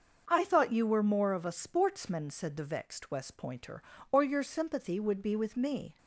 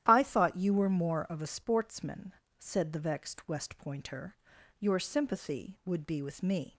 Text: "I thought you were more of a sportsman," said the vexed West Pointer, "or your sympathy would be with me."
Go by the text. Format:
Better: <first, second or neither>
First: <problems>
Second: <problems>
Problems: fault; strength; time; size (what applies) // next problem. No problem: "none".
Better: first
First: starts louder than the rest; until 1.3 s; 6.5 dB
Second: starts louder than the rest; strong; until 1.0 s; 11.5 dB // skips "or"; at 4.5 s